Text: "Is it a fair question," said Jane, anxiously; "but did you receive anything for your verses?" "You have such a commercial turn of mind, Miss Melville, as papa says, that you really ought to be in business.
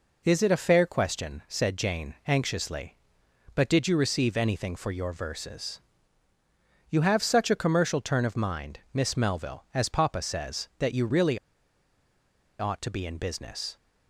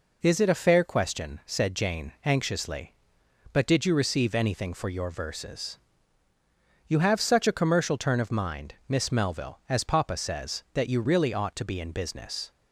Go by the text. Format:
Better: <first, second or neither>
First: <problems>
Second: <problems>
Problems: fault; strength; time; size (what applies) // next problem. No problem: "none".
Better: second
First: pauses between "really" and "ought"; at 11.3 s; 1.2 s long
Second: none